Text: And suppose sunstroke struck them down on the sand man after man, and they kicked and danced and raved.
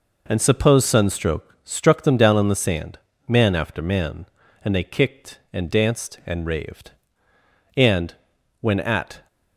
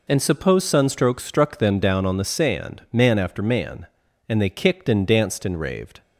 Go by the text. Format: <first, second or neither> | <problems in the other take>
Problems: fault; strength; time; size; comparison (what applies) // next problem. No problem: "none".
second | pauses between "sand" and "man"; slight; at 2.9 s; 0.30 s long // goes on to say "And when at"; from 7.7 s on; 1.5 s long